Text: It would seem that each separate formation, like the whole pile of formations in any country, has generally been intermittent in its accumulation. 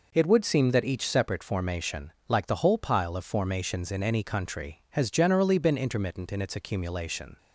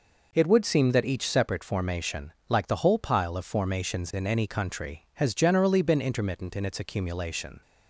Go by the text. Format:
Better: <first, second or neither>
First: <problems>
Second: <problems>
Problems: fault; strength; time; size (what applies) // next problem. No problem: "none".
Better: neither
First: none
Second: none